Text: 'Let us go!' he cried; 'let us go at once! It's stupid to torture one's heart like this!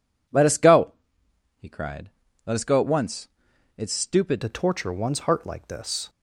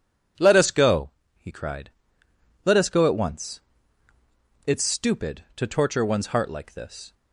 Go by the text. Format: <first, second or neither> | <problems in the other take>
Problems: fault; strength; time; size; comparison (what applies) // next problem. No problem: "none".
second | changes voice at "to"; from 4.4 s on; 1.6 s long